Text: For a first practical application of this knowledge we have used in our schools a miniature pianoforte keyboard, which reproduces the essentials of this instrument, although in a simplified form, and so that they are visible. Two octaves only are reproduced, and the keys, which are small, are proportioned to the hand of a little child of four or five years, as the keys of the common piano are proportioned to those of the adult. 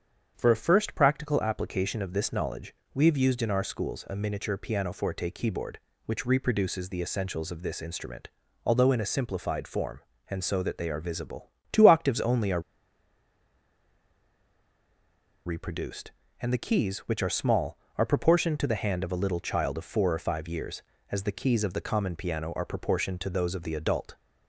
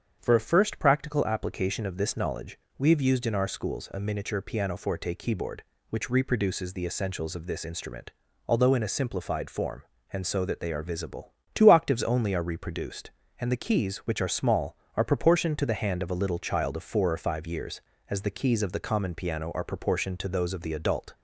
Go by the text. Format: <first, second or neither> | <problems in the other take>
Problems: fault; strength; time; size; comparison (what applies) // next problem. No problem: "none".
second | starts louder than the rest; strong; until 1.3 s; 7.5 dB; strong in the second // pauses between "knowledge" and "we"; slight; at 2.7 s; 0.20 s long; slight in the second // pauses between "are" and "reproduced"; strong; at 12.5 s; 2.8 s long